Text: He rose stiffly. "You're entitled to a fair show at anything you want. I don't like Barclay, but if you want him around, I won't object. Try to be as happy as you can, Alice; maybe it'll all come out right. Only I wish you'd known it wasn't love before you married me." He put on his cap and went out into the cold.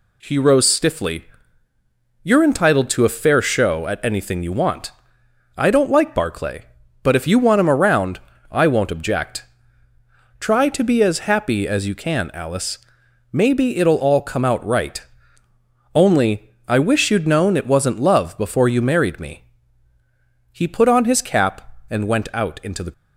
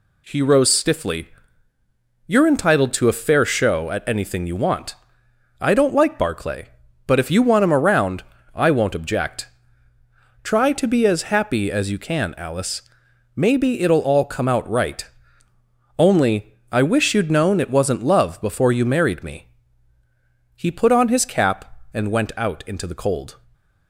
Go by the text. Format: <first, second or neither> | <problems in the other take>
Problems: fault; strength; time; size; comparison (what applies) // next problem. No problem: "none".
second | pauses between "Only" and "I"; slight; at 16.5 s; 0.16 s long; slight in the second // stops before "cold"; at 22.9 s